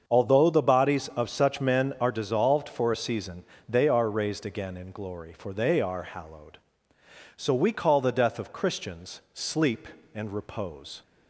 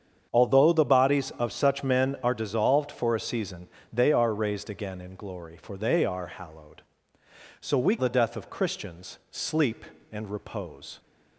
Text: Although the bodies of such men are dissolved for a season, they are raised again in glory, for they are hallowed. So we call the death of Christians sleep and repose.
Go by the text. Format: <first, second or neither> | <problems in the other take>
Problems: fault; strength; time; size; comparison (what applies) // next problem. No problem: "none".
first | starts louder than the rest; strong; until 1.3 s; 7.5 dB; also in the first // skips "call"; at 7.9 s